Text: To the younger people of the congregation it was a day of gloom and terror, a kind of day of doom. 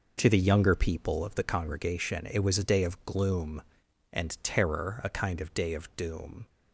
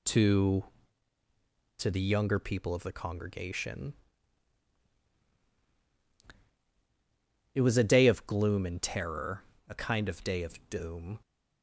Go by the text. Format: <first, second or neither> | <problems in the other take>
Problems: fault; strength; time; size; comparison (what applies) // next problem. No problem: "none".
first | says "To" twice; at 1.7 s // pauses between "congregation" and "it"; strong; at 3.9 s; 3.6 s long